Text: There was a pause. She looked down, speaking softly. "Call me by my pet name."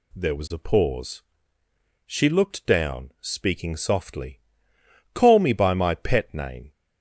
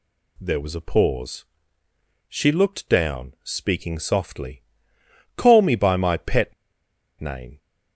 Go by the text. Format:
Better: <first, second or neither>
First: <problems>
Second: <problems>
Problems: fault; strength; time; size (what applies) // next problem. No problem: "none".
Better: first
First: none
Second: pauses between "pet" and "name"; noticeable; at 6.5 s; 0.66 s long